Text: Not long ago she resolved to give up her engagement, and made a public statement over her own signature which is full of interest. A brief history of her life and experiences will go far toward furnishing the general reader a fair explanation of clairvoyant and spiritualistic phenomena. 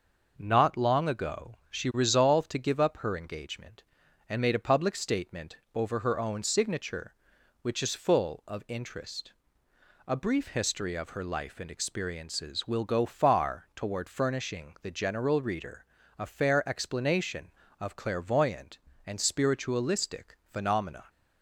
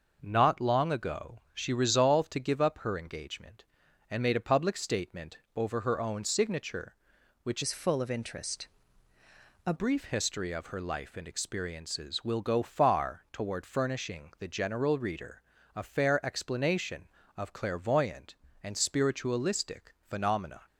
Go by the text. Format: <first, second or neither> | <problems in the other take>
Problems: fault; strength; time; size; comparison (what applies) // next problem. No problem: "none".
first | starts louder than the rest; noticeable; until 1.2 s; 6 dB // pauses between "statement" and "over"; slight; at 5.3 s; 0.16 s long; slight in the first // changes voice from "is" to "A"; from 7.6 to 9.7 s; 2.1 s long // pauses between "reader" and "a"; slight; at 15.4 s; 0.34 s long; slight in the first